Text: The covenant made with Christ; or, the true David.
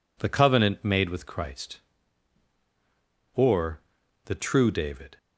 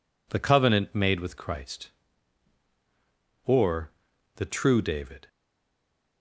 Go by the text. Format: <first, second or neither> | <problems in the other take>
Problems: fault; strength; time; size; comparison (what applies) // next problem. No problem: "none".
first | stays silent after the last word; slight; from 5.2 s on; 1.0 s long